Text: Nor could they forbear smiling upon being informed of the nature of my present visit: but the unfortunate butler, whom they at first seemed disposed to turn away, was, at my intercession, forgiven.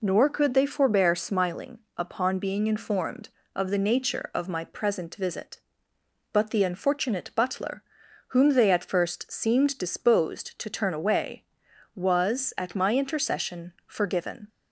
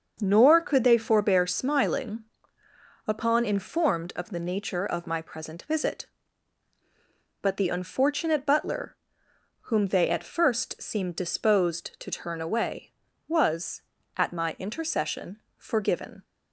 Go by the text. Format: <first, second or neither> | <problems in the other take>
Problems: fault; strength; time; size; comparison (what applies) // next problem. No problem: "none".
first | starts louder than the rest; until 1.2 s; 6.5 dB // pauses between "smiling" and "upon"; noticeable; at 2.2 s; 0.82 s long; slight in the first // skips "being"; at 3.4 s